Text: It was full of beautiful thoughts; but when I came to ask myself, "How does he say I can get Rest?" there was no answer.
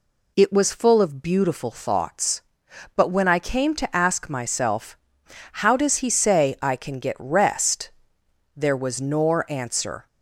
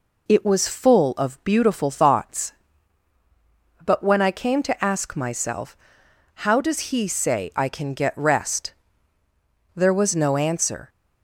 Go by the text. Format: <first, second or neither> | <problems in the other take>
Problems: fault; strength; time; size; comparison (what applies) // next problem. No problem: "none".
second | says "nor" for "no"; at 8.9 s